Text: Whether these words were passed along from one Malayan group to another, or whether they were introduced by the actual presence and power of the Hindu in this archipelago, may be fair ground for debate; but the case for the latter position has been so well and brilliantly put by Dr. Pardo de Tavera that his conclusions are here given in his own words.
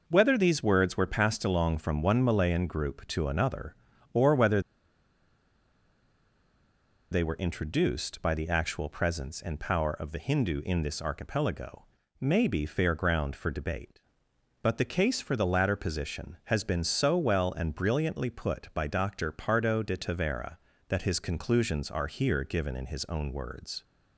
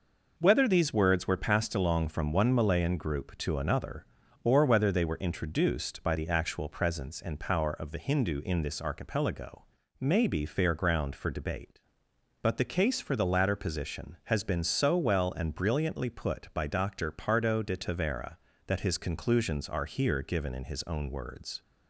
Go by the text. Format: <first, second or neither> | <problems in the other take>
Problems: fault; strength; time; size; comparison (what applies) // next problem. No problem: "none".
second | pauses between "whether" and "they"; strong; at 4.6 s; 2.5 s long